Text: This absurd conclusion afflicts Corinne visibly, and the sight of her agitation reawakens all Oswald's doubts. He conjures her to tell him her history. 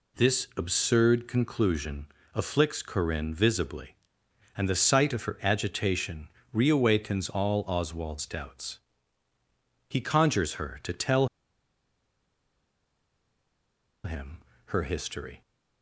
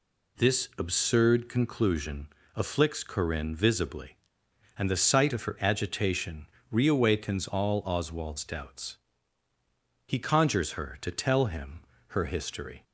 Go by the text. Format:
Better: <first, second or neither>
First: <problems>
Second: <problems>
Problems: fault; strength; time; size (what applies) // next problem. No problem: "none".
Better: second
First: pauses between "conclusion" and "afflicts"; slight; at 2.0 s; 0.28 s long // pauses between "agitation" and "reawakens"; slight; at 6.2 s; 0.26 s long // pauses between "tell" and "him"; strong; at 11.2 s; 2.7 s long // pauses between "him" and "her"; slight; at 14.3 s; 0.28 s long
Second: pauses between "conclusion" and "afflicts"; slight; at 2.2 s; 0.28 s long // pauses between "agitation" and "reawakens"; slight; at 6.4 s; 0.26 s long // pauses between "him" and "her"; slight; at 11.8 s; 0.28 s long